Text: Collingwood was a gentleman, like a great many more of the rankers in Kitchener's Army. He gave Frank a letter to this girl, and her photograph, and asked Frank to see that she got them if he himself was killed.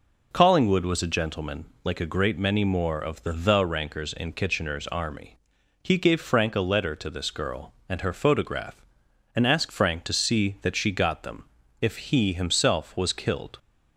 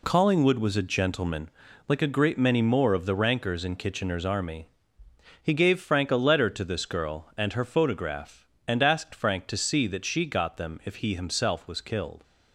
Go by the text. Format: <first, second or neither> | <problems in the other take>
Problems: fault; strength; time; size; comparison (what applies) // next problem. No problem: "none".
second | says "the" twice; at 3.3 s // pauses between "them" and "if"; at 11.4 s; 0.38 s long